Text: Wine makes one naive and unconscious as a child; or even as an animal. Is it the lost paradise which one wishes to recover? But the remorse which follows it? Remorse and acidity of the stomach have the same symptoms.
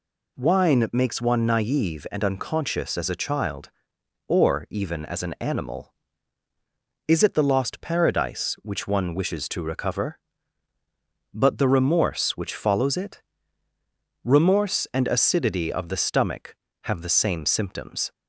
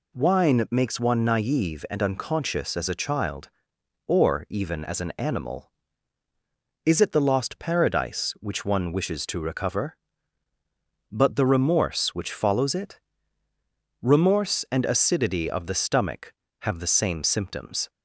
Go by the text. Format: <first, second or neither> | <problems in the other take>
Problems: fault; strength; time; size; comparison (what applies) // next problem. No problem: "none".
neither | none